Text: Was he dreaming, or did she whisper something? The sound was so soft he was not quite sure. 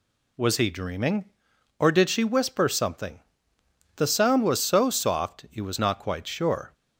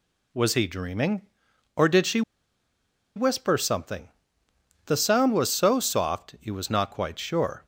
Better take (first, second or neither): first